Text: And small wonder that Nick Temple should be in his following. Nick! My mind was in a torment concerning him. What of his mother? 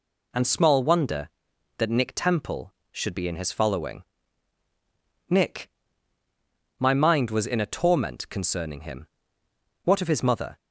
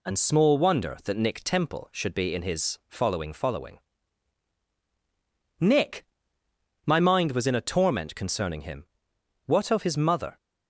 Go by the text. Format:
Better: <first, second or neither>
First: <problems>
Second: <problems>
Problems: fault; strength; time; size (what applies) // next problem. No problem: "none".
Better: first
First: none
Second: says "following" twice; at 3.3 s